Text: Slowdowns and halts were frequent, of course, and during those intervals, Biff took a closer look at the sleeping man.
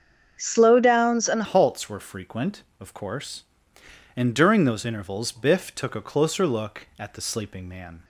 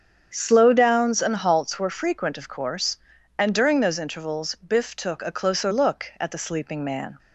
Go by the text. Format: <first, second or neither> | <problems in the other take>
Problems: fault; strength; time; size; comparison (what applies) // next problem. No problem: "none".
second | starts louder than the rest; strong; until 1.4 s; 7 dB; strong in the second // changes voice at "halts"; from 1.4 s on; 6.6 s long